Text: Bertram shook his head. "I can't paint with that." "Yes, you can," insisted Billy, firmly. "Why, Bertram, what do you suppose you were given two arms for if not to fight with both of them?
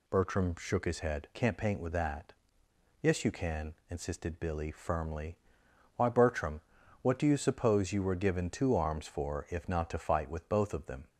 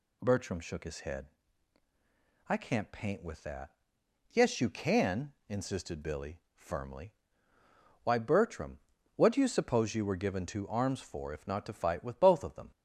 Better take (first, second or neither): second